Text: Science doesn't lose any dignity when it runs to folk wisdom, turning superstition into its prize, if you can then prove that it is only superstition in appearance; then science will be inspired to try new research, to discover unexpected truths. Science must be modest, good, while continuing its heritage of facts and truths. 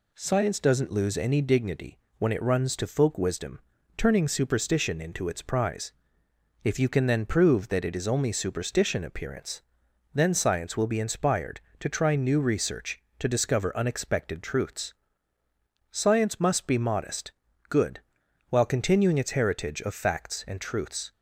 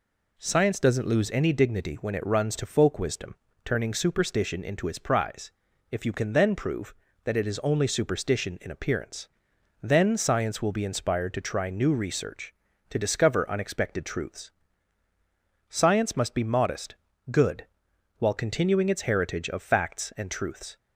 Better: second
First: pauses between "dignity" and "when"; slight; at 1.9 s; 0.20 s long // skips "in"; at 9.0 s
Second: none

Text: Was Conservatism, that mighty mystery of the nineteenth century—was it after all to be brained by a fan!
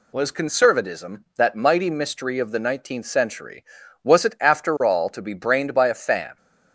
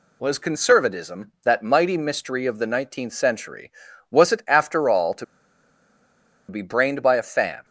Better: first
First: none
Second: pauses between "to" and "be"; at 5.2 s; 1.2 s long

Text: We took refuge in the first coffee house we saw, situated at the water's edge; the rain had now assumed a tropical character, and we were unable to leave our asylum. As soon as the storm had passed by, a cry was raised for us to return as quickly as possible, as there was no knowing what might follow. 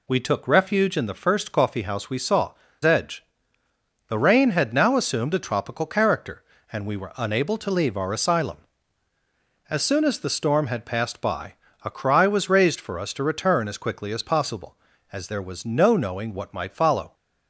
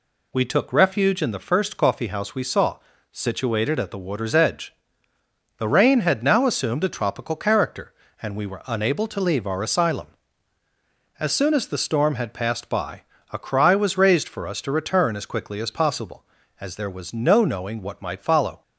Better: second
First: skips "situated at the water's"; at 2.6 s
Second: none

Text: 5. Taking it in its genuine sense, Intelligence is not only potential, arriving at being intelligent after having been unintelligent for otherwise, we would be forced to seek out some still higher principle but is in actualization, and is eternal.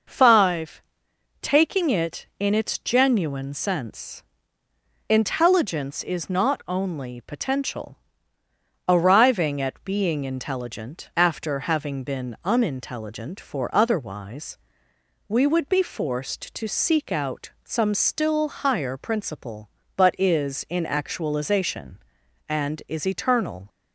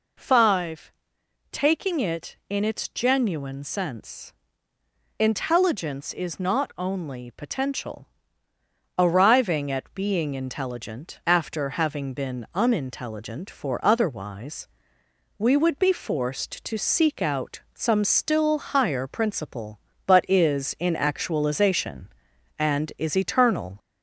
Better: first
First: none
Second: gets louder; slight; throughout; 2.5 dB

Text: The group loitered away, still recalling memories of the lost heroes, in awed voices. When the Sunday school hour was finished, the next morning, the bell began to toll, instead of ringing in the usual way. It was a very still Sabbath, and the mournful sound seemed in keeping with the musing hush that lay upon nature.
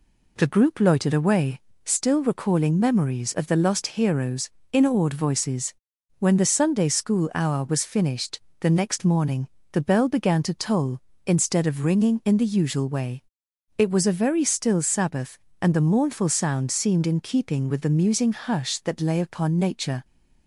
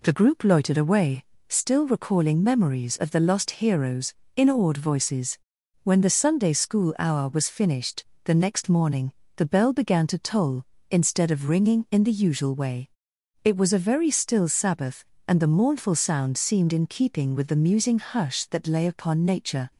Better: neither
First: none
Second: none

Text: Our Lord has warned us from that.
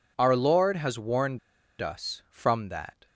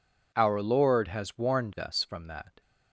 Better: second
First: pauses between "warned" and "us"; at 1.3 s; 0.43 s long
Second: none

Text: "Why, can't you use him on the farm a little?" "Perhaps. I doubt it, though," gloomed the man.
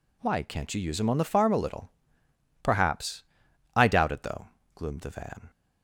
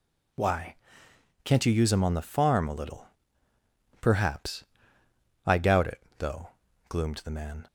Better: second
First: says "van" for "man"; at 5.0 s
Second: none

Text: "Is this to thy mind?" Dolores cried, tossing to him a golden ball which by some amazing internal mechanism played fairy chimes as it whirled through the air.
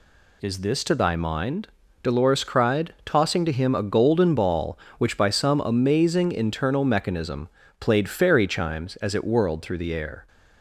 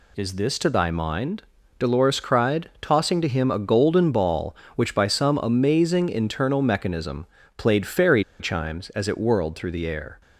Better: first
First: pauses between "mechanism" and "played"; slight; at 7.4 s; 0.30 s long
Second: pauses between "mechanism" and "played"; slight; at 7.2 s; 0.30 s long // pauses between "fairy" and "chimes"; slight; at 8.2 s; 0.17 s long

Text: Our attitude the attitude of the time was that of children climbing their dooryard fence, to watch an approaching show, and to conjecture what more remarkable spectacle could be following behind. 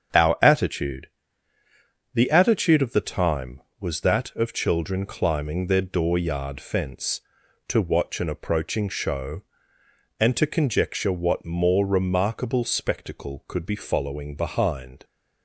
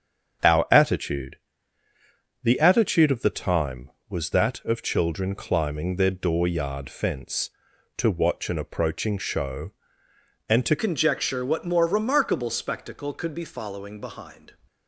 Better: first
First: starts louder than the rest; strong; until 2.2 s; 7.5 dB // pauses between "attitude" and "the"; at 1.0 s; 1.0 s long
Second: starts louder than the rest; strong; until 2.5 s; 7.5 dB // pauses between "attitude" and "the"; at 1.3 s; 1.0 s long // changes voice at "conjecture"; from 10.7 s on; 3.8 s long

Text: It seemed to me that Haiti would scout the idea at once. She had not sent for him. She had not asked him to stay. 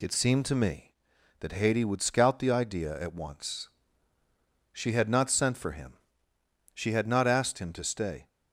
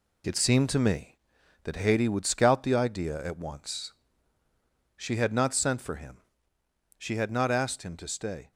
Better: first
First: none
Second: gets quieter; noticeable; throughout; 6 dB

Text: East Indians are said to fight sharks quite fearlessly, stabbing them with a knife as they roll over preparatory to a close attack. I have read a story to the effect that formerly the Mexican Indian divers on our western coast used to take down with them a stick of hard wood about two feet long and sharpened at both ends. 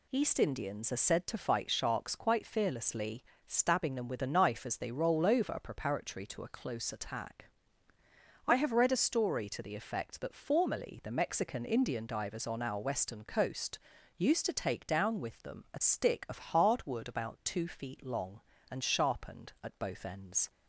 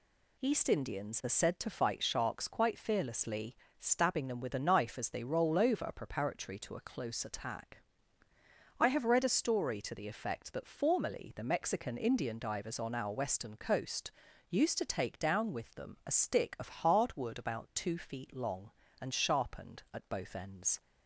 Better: neither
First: pauses between "coast" and "used"; slight; at 13.7 s; 0.36 s long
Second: pauses between "coast" and "used"; slight; at 14.1 s; 0.36 s long

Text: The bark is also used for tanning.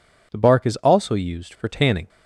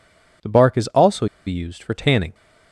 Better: first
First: none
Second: pauses between "also" and "used"; slight; at 1.2 s; 0.20 s long

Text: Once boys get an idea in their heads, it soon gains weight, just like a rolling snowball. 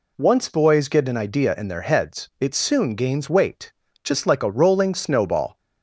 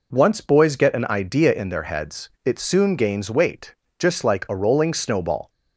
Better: neither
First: none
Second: none

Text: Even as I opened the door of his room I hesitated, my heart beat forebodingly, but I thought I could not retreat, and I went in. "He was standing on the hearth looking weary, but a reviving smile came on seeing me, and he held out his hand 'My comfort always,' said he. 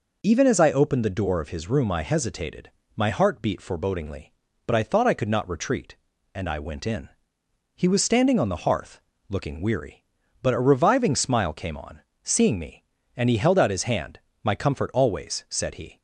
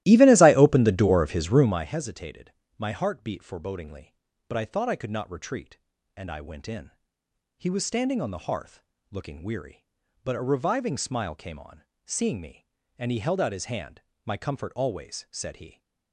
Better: first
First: pauses between "hearth" and "looking"; slight; at 8.9 s; 0.30 s long // pauses between "on" and "seeing"; slight; at 12.0 s; 0.22 s long // pauses between "hand" and "My"; slight; at 14.1 s; 0.24 s long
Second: starts louder than the rest; strong; until 1.9 s; 15.5 dB // pauses between "hearth" and "looking"; slight; at 8.8 s; 0.30 s long // pauses between "on" and "seeing"; slight; at 11.8 s; 0.22 s long // pauses between "hand" and "My"; slight; at 13.9 s; 0.24 s long

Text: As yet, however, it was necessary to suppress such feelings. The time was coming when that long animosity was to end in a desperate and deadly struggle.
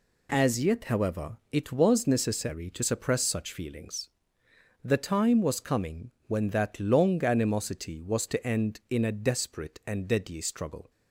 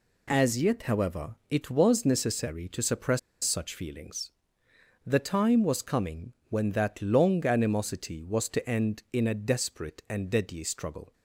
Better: first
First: pauses between "coming" and "when"; slight; at 6.1 s; 0.16 s long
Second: pauses between "suppress" and "such"; slight; at 3.1 s; 0.24 s long // pauses between "coming" and "when"; slight; at 6.3 s; 0.16 s long

